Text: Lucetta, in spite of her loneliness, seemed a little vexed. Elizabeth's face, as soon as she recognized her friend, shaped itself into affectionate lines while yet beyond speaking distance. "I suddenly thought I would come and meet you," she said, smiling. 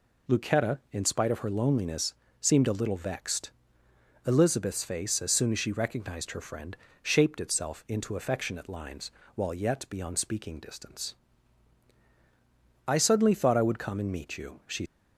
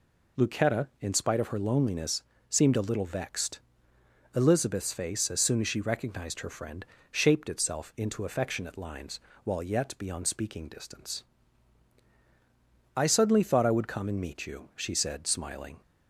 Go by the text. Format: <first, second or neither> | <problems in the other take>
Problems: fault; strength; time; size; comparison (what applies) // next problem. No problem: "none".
second | pauses between "lines" and "while"; slight; at 9.1 s; 0.24 s long; slight in the second // stops before "said smiling"; at 14.8 s